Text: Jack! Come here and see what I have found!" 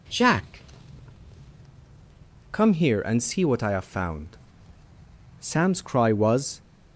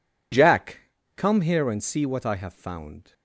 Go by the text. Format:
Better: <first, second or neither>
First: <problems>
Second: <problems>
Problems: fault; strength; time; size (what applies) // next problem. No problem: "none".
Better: second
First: goes on to say "Sam's cry was"; noticeable; from 5.4 s on; 1.2 s long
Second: none